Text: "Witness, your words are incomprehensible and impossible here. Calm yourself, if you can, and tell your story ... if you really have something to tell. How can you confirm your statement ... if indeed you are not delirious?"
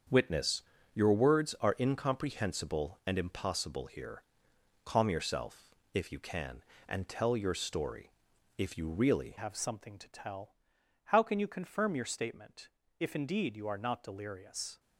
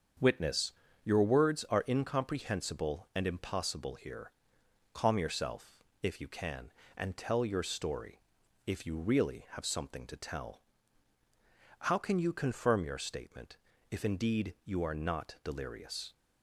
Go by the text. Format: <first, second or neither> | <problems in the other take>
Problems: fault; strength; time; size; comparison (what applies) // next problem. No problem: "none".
second | starts louder than the rest; strong; until 1.4 s; 7 dB; also in the second // changes voice at "have"; from 9.3 s on; 5.4 s long